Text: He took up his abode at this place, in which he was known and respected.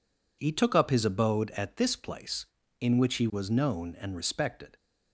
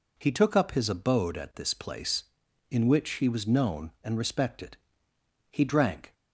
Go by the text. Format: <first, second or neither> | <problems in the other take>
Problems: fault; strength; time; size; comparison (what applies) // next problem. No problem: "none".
first | goes on to say "He drank"; noticeable; from 5.5 s on; 0.62 s long